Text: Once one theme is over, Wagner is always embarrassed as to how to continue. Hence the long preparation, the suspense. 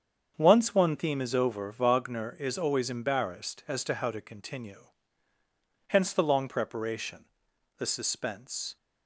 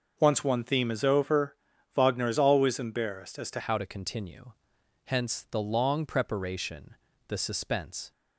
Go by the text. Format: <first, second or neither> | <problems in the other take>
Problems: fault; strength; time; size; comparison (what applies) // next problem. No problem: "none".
first | starts louder than the rest; noticeable; until 1.1 s; 6 dB; strong in the first // changes voice at "how"; from 3.5 s on; 4.6 s long